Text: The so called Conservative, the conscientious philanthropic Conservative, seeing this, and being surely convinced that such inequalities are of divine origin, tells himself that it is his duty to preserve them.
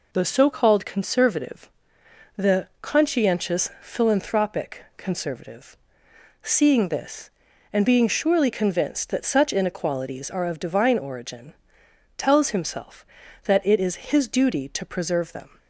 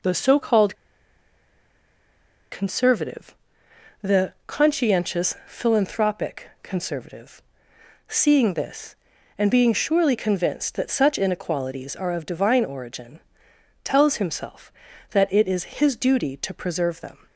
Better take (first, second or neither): first